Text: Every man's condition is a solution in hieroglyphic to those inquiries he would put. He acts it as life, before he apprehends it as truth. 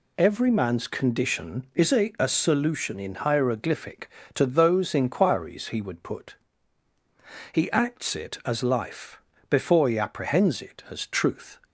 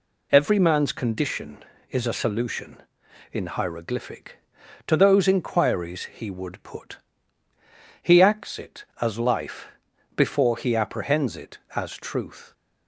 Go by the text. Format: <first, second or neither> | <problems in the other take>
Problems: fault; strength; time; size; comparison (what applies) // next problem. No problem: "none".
second | says "a" twice; at 2.1 s